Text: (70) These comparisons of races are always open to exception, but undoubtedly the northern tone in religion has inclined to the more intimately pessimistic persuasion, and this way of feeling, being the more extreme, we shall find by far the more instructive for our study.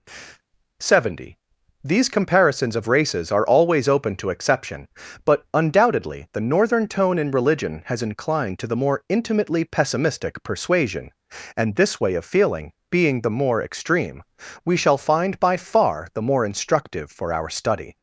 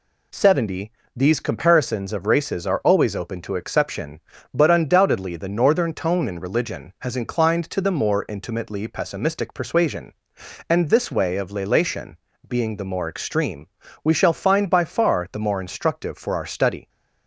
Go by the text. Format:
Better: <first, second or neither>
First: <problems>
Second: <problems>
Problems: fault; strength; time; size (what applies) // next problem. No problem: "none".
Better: first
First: none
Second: says "lelation" for "feeling"; at 11.5 s